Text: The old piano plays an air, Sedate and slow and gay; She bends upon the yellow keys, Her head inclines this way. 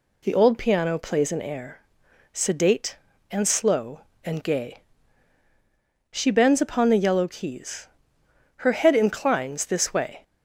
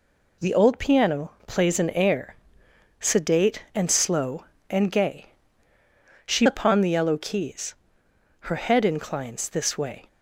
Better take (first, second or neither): first